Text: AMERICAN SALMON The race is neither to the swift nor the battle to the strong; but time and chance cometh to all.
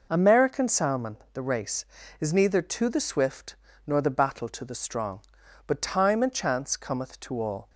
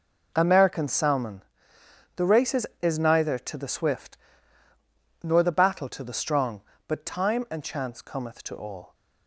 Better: first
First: pauses between "SALMON" and "The"; slight; at 1.1 s; 0.16 s long // pauses between "swift" and "nor"; slight; at 3.5 s; 0.32 s long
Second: pauses between "SALMON" and "The"; noticeable; at 1.4 s; 0.72 s long // says "is" twice; at 2.8 s // pauses between "swift" and "nor"; at 4.1 s; 1.0 s long

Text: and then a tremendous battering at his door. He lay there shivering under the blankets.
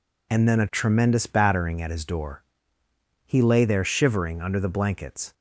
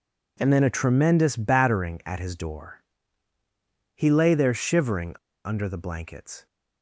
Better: first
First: none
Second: pauses between "shivering" and "under"; slight; at 5.1 s; 0.28 s long

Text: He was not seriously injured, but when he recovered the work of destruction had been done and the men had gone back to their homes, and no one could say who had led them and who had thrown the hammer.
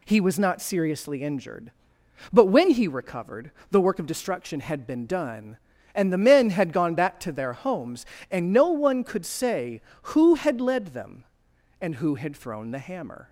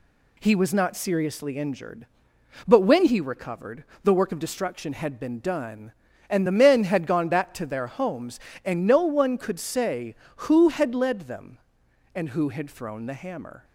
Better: neither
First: pauses between "recovered" and "the"; slight; at 3.5 s; 0.20 s long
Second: pauses between "recovered" and "the"; slight; at 3.8 s; 0.20 s long

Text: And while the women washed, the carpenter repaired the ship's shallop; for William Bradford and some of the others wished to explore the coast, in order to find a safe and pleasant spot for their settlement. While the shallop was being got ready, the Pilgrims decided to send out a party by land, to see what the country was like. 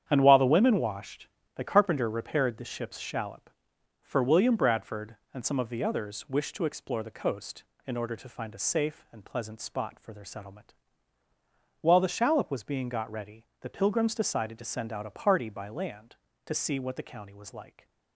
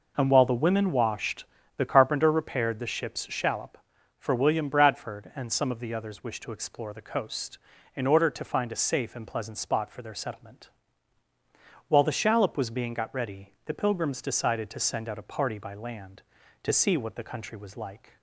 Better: second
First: starts louder than the rest; strong; until 1.0 s; 9 dB // says "county" for "country"; at 17.0 s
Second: none

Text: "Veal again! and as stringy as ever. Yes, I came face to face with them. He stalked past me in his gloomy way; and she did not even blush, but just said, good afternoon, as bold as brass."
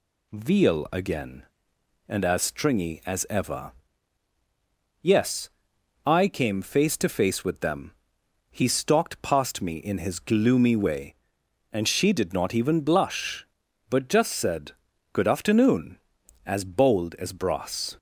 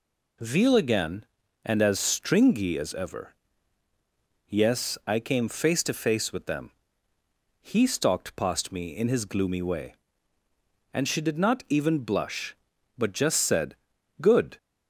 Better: first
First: none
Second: stops before "afternoon as bold as brass"; at 14.5 s

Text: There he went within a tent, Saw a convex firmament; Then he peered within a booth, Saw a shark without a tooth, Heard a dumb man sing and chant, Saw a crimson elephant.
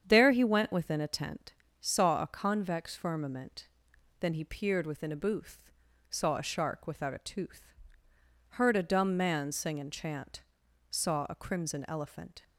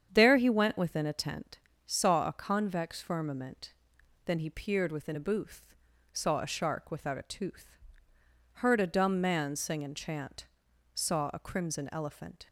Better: neither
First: starts louder than the rest; strong; until 1.0 s; 8 dB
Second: starts louder than the rest; strong; until 1.1 s; 8 dB

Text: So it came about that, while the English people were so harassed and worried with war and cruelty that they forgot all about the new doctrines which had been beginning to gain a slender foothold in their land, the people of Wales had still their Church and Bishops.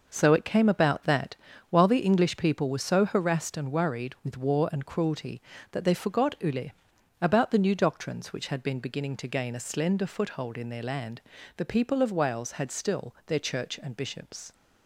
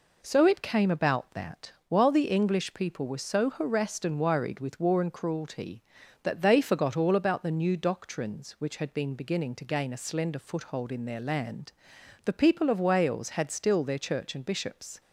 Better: second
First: says "ule" for "all"; at 6.3 s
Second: none

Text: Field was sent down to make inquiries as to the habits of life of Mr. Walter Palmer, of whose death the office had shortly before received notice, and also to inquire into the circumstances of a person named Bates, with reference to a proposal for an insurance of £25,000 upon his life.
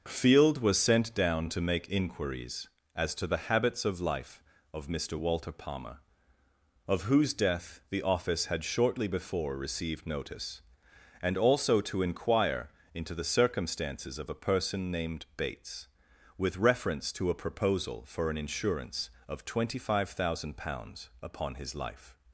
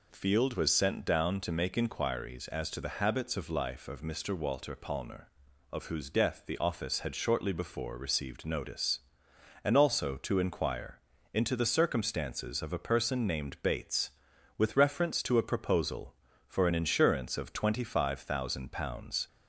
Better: first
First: pauses between "inquire" and "into"; slight; at 12.6 s; 0.24 s long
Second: pauses between "inquire" and "into"; slight; at 10.9 s; 0.32 s long // stops before "upon his life"; at 19.2 s

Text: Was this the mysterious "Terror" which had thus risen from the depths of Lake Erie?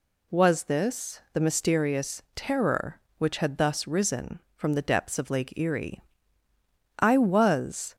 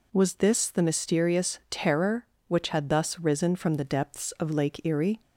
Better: second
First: goes on to say "I was"; noticeable; from 6.9 s on; 0.96 s long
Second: none

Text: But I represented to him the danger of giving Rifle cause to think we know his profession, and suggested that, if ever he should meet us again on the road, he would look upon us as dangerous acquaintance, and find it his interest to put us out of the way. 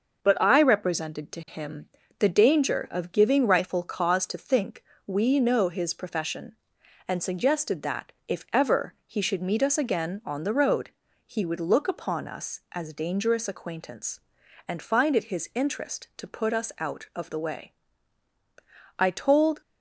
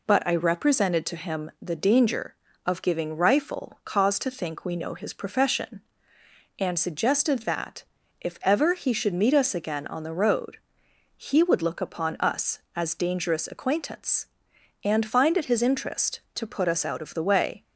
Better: second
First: starts louder than the rest; noticeable; until 1.2 s; 6 dB // pauses between "him" and "the"; slight; at 1.8 s; 0.32 s long // pauses between "think" and "we"; slight; at 4.8 s; 0.24 s long // goes on to say "I told"; noticeable; from 18.9 s on; 0.62 s long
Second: none

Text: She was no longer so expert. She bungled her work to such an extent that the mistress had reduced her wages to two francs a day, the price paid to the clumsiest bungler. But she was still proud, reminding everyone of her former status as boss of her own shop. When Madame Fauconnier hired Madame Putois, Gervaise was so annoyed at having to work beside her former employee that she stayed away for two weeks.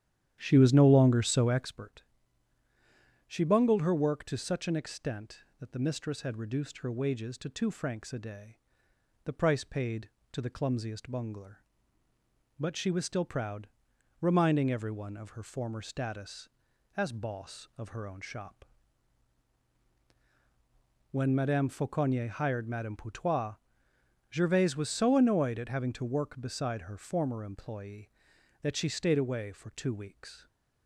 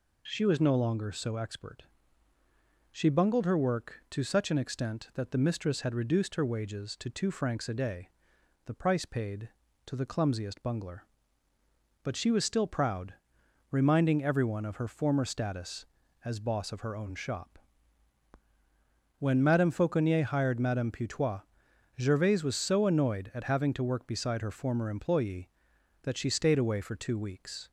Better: second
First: starts louder than the rest; strong; until 1.8 s; 10.5 dB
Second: none

